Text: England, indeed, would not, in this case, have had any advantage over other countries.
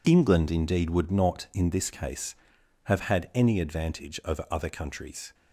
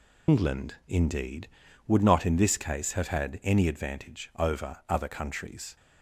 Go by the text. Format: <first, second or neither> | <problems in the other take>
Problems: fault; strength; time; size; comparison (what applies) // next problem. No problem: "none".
first | loses the start of "England"; at 0.2 s; 125 ms